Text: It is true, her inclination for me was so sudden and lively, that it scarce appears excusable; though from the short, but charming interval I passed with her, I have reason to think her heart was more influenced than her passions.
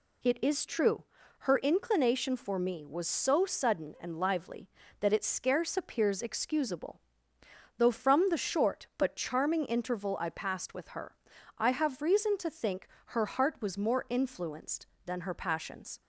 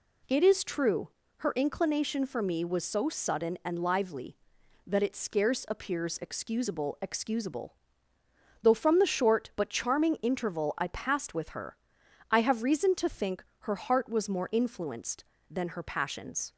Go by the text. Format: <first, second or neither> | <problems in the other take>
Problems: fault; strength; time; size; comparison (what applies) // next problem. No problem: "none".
first | says "excusable" twice; at 7.0 s // pauses between "think" and "her"; slight; at 13.4 s; 0.18 s long; slight in the first